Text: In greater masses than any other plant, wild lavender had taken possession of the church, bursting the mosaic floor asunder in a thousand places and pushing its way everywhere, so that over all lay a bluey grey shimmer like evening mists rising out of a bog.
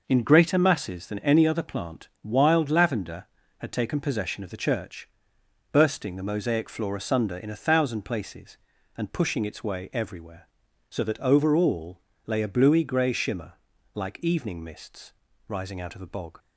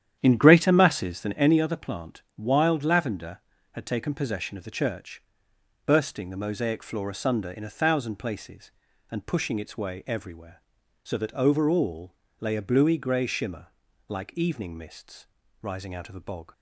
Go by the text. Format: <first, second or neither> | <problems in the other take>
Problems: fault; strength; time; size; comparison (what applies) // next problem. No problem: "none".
first | starts louder than the rest; strong; until 1.5 s; 10 dB // pauses between "all" and "lay"; slight; at 12.1 s; 0.26 s long; slight in the first // pauses between "shimmer" and "like"; at 13.6 s; 0.40 s long; also in the first // pauses between "mists" and "rising"; slight; at 15.2 s; 0.36 s long; slight in the first